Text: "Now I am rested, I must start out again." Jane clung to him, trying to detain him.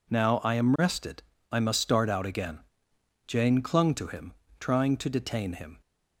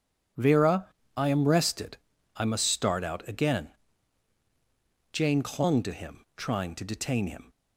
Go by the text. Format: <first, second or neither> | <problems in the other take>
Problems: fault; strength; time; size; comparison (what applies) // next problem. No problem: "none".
first | says "Vera" for "Now"; at 0.3 s